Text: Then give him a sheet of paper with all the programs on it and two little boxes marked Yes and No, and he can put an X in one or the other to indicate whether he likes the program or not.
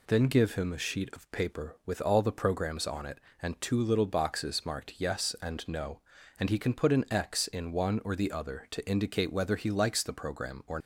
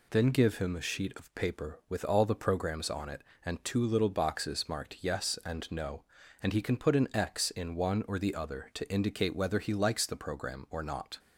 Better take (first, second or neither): second